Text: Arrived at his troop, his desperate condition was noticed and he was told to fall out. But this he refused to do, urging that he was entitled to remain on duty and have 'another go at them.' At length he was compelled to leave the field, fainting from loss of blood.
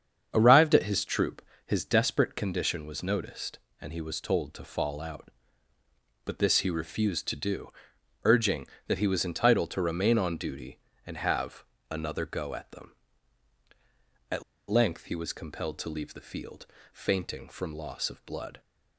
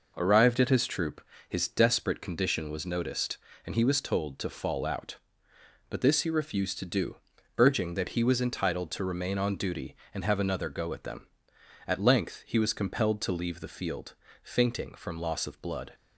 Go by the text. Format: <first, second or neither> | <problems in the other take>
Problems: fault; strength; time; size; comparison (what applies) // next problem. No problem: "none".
second | starts louder than the rest; strong; until 1.3 s; 7.5 dB // pauses between "have" and "another"; slight; at 11.6 s; 0.26 s long // pauses between "At" and "length"; slight; at 14.4 s; 0.26 s long